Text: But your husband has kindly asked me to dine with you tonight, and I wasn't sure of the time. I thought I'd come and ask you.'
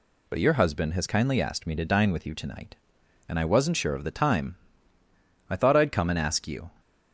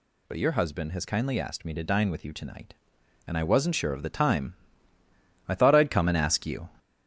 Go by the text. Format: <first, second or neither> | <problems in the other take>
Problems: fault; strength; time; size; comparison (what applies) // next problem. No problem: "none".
first | gets louder; noticeable; throughout; 5 dB